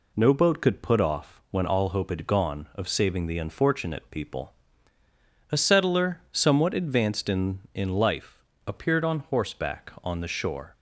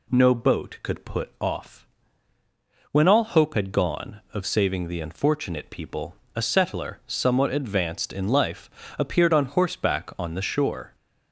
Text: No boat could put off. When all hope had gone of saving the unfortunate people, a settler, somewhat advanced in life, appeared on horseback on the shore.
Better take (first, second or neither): second